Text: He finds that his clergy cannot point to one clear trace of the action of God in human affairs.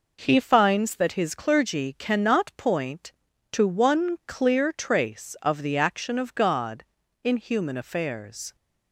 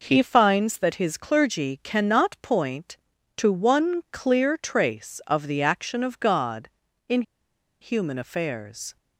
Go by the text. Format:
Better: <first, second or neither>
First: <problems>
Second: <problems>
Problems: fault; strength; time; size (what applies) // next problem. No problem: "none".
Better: first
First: none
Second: pauses between "in" and "human"; noticeable; at 7.2 s; 0.59 s long